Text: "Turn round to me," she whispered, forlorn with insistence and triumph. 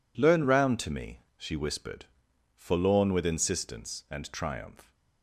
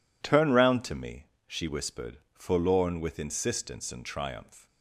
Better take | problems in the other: second | says "Learn" for "Turn"; at 0.1 s

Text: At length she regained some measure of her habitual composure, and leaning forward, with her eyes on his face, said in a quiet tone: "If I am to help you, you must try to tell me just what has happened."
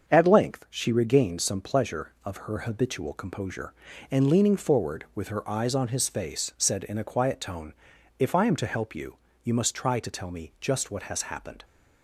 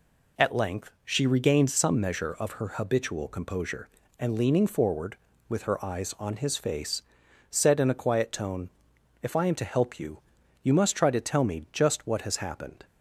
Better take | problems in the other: second | starts louder than the rest; until 1.1 s; 7 dB // says "pleasure" for "measure"; at 1.6 s

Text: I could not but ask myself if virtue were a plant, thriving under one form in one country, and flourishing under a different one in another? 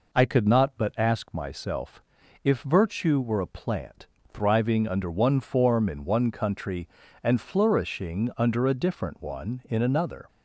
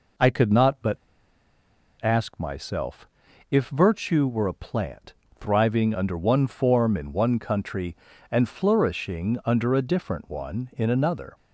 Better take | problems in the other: first | pauses between "but" and "ask"; at 0.9 s; 1.0 s long // pauses between "myself" and "if"; at 3.0 s; 0.42 s long; also in the first

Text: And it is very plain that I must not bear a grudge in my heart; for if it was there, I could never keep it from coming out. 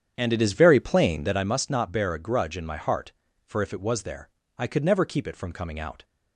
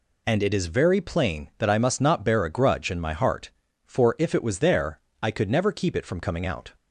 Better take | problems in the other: second | starts louder than the rest; strong; until 1.6 s; 8.5 dB

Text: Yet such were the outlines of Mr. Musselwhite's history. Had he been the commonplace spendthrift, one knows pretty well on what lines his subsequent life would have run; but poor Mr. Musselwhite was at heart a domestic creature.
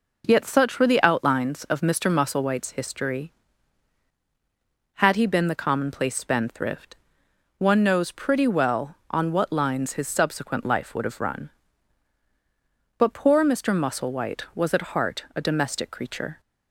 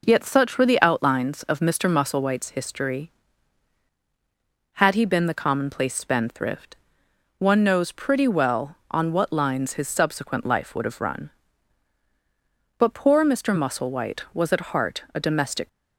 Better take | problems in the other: first | stops before "creature"; at 15.6 s

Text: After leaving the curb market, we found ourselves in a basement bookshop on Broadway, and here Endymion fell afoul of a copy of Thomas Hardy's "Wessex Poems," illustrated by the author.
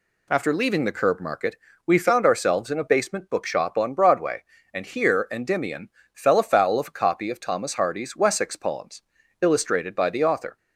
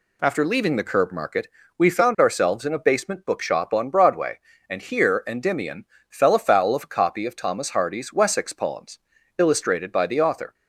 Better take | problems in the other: neither | pauses between "Endymion" and "fell"; slight; the same in both

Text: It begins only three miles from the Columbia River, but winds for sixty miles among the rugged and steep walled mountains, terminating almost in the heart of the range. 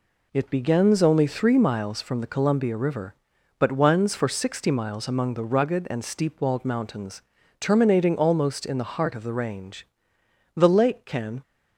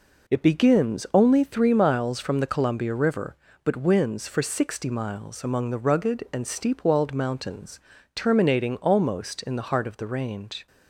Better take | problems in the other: second | goes on to say "The lake can"; noticeable; from 10.5 s on; 0.86 s long

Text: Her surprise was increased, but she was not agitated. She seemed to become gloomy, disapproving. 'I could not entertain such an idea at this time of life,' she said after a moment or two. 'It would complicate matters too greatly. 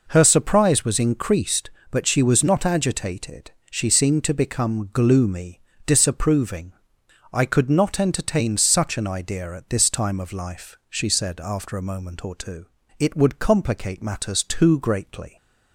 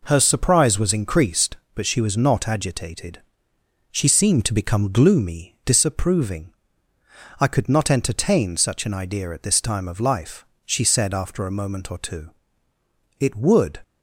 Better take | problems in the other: first | stops before "complicate matters too greatly"; at 13.8 s

